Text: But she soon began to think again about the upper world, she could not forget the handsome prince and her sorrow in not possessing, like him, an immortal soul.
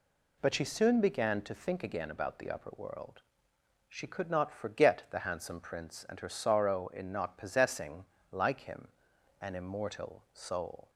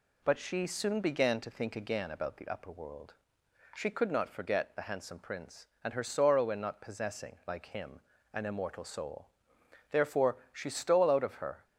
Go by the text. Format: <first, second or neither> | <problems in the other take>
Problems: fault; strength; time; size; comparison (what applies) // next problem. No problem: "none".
first | goes on to say "Therefore she stole out of her"; strong; from 9.9 s on; 1.7 s long